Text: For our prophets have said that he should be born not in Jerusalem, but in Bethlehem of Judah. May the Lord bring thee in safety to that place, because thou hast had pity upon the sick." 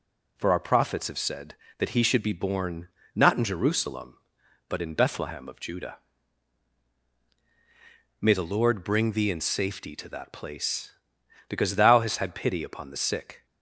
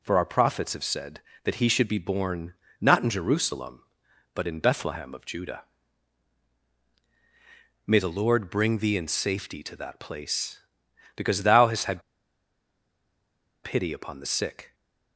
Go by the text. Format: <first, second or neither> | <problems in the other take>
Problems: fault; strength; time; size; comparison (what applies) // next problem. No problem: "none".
first | pauses between "born" and "not"; slight; at 2.5 s; 0.26 s long; slight in the first // pauses between "had" and "pity"; strong; at 12.0 s; 1.6 s long